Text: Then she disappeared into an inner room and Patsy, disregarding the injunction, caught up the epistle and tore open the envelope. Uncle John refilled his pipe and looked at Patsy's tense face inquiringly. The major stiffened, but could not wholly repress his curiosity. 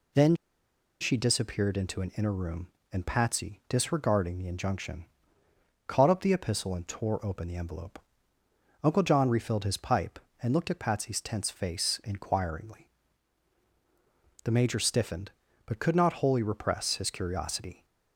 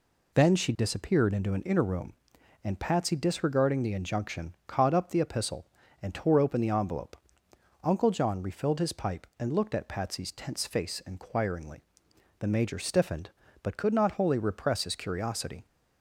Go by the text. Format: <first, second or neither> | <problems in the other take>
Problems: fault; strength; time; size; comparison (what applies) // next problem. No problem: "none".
second | pauses between "Then" and "she"; noticeable; at 0.3 s; 0.65 s long